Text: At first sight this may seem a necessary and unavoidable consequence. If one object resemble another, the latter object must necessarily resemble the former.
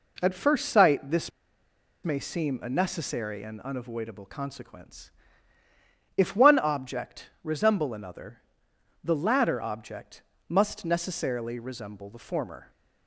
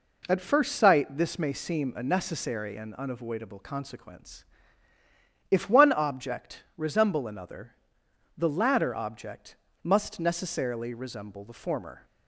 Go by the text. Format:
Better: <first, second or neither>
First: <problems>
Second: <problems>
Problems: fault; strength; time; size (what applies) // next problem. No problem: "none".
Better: second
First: pauses between "this" and "may"; noticeable; at 1.3 s; 0.73 s long // pauses between "object" and "must"; slight; at 10.2 s; 0.26 s long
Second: pauses between "object" and "must"; slight; at 9.5 s; 0.27 s long